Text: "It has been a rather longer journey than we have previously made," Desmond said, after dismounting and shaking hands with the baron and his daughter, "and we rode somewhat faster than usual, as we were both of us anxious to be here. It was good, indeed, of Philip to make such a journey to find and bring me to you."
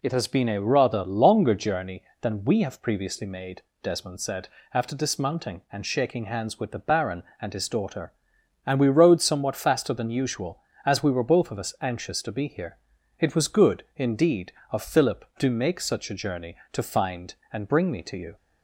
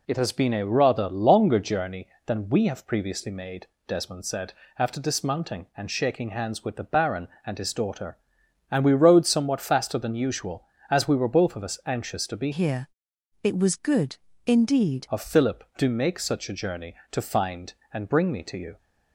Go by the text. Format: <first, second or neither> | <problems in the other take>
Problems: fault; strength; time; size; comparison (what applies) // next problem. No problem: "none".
first | changes voice from "here" to "indeed"; from 12.5 to 15.0 s; 2.5 s long